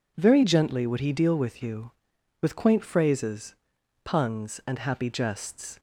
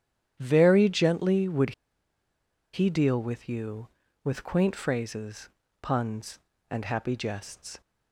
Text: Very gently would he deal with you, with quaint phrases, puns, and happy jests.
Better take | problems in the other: first | starts louder than the rest; strong; until 1.4 s; 10 dB // pauses between "would" and "he"; at 1.7 s; 1.0 s long

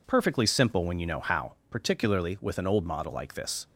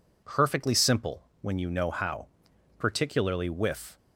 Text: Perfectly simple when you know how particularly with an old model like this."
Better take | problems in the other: first | pauses between "simple" and "when"; slight; at 1.2 s; 0.18 s long // pauses between "how" and "particularly"; noticeable; at 2.2 s; 0.52 s long; slight in the first // stops before "an old model like this"; at 3.9 s

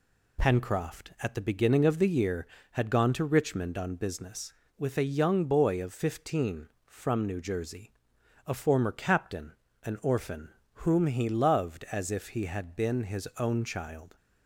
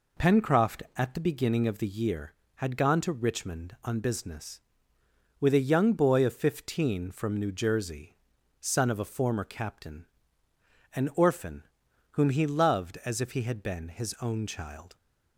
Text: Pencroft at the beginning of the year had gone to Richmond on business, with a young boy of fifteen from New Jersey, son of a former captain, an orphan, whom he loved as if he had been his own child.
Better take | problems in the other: second | skips "son of"; at 8.1 s

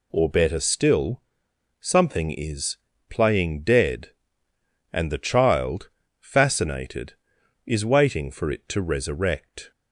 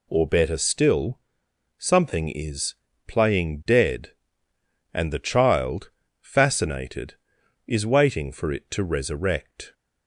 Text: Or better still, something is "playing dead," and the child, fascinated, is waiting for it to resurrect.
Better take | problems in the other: neither | pauses between "is" and "playing"; slight; the same in both

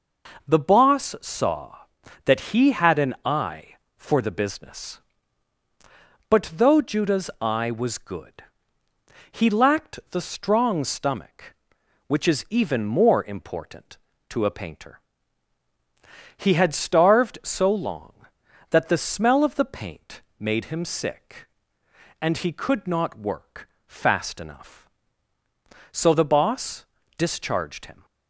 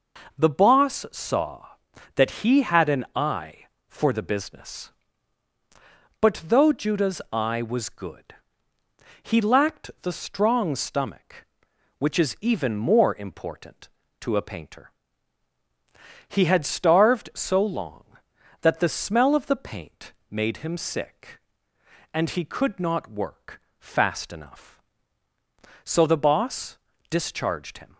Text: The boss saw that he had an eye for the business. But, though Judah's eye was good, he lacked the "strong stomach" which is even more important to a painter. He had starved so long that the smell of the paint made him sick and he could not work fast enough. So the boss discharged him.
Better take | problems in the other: neither | pauses between "paint" and "made"; slight; the same in both // pauses between "work" and "fast"; slight; the same in both // pauses between "boss" and "discharged"; slight; the same in both

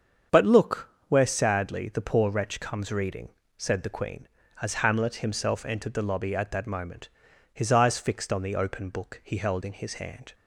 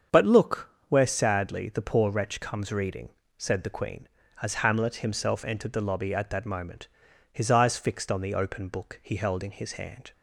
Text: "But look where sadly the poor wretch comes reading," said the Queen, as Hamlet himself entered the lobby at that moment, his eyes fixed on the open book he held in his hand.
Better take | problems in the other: neither | starts louder than the rest; strong; the same in both // pauses between "look" and "where"; slight; the same in both

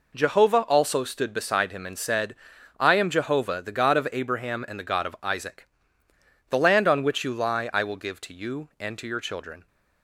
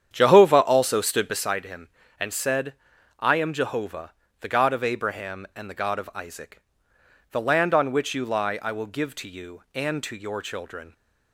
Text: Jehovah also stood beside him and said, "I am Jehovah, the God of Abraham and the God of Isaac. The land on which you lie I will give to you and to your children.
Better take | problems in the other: first | starts louder than the rest; strong; until 1.4 s; 9 dB

